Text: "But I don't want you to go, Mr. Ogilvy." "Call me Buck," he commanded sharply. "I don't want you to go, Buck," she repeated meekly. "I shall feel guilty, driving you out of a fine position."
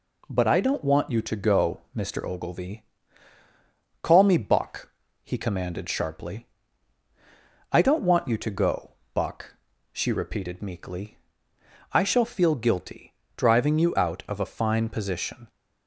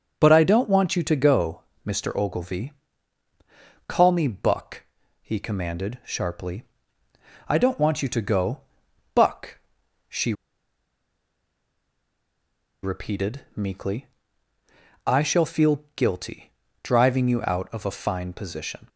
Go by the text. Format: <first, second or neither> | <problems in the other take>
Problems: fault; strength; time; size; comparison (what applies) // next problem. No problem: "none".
first | starts louder than the rest; until 1.1 s; 6.5 dB // pauses between "she" and "repeated"; strong; at 10.3 s; 2.5 s long